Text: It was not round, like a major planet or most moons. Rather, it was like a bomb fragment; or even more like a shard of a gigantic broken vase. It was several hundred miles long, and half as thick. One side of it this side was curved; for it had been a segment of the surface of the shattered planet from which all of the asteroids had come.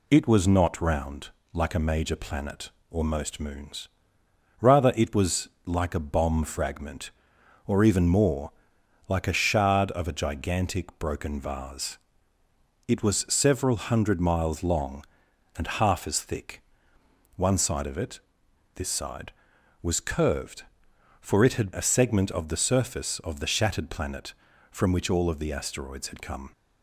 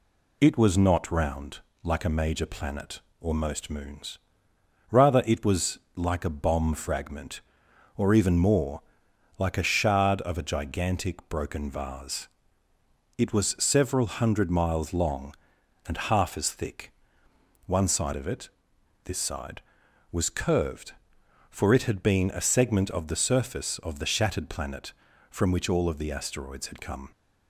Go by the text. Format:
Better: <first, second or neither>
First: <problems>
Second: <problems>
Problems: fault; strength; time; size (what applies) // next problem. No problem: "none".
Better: second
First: pauses between "was" and "like"; slight; at 5.4 s; 0.16 s long // pauses between "more" and "like"; noticeable; at 8.5 s; 0.58 s long // pauses between "it" and "this"; noticeable; at 18.1 s; 0.56 s long // skips "been"; at 21.7 s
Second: pauses between "was" and "like"; slight; at 5.7 s; 0.16 s long // pauses between "more" and "like"; noticeable; at 8.8 s; 0.58 s long // pauses between "it" and "this"; noticeable; at 18.4 s; 0.56 s long